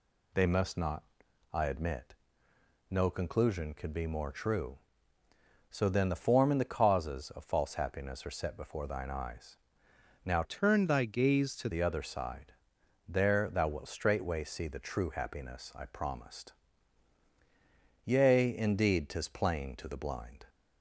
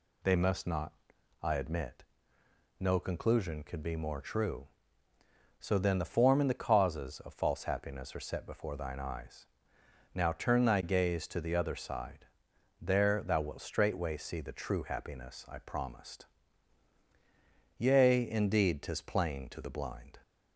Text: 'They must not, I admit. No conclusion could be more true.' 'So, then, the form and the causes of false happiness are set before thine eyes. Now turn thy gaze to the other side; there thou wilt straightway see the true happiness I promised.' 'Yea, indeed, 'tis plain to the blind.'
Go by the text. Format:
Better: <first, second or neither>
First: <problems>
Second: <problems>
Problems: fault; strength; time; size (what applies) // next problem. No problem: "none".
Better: second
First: changes voice from "turn" to "to"; from 10.4 to 11.6 s; 1.2 s long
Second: none